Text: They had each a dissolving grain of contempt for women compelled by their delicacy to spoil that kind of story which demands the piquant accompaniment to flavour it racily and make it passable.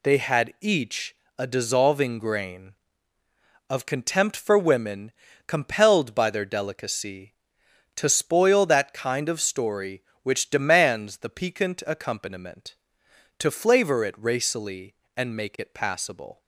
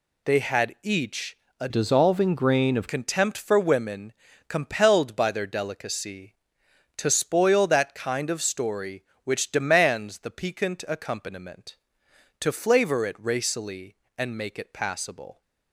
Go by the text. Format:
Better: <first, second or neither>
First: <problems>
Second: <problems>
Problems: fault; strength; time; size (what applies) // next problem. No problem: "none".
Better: first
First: pauses between "each" and "a"; slight; at 1.1 s; 0.22 s long // pauses between "women" and "compelled"; slight; at 5.1 s; 0.34 s long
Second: pauses between "each" and "a"; slight; at 1.3 s; 0.22 s long // changes voice from "dissolving" to "of"; from 1.6 to 2.8 s; 1.2 s long // pauses between "women" and "compelled"; slight; at 4.1 s; 0.34 s long